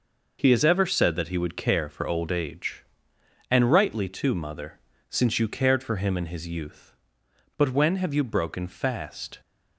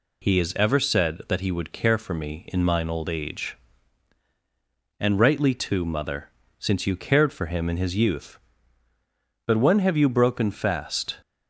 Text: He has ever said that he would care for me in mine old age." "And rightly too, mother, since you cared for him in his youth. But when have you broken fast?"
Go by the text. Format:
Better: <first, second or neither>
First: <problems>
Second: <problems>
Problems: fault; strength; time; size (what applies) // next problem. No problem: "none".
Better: second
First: skips "me in mine"; at 2.0 s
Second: none